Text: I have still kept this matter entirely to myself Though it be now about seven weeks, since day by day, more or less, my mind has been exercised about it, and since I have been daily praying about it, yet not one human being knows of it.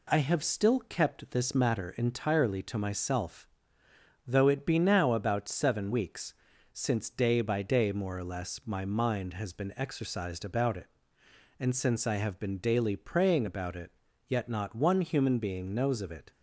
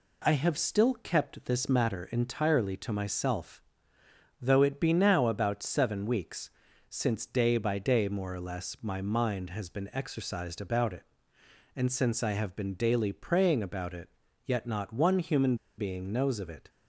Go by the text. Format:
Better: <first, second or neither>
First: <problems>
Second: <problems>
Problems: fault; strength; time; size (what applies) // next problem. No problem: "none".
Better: first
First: pauses between "myself" and "Though"; noticeable; at 3.4 s; 0.80 s long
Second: pauses between "myself" and "Though"; noticeable; at 3.6 s; 0.80 s long // pauses between "human" and "being"; slight; at 15.5 s; 0.23 s long